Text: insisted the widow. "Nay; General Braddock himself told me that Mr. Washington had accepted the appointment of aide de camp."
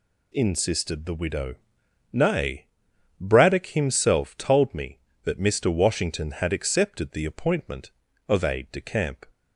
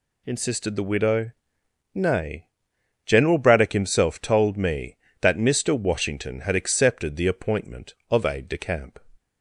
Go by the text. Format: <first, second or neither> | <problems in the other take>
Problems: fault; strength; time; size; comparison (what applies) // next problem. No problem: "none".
second | skips "General"; at 2.9 s